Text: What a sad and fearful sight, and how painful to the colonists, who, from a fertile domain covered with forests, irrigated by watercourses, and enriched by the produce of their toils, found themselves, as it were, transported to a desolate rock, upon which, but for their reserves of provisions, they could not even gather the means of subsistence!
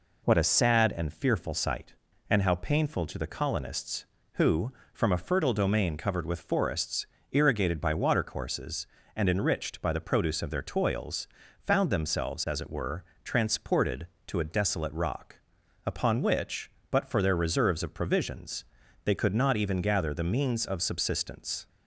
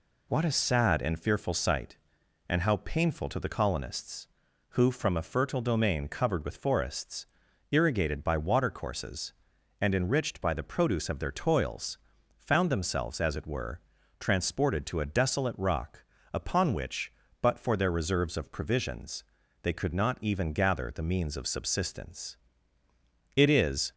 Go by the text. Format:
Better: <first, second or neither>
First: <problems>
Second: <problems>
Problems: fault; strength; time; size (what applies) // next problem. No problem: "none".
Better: first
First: none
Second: goes on to say "It is"; from 23.3 s on; 0.58 s long